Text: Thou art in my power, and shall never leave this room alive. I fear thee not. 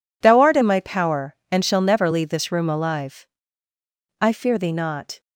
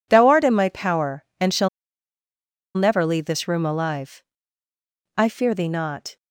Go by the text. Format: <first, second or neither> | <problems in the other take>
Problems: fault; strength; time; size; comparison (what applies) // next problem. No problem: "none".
first | pauses between "shall" and "never"; at 1.6 s; 1.0 s long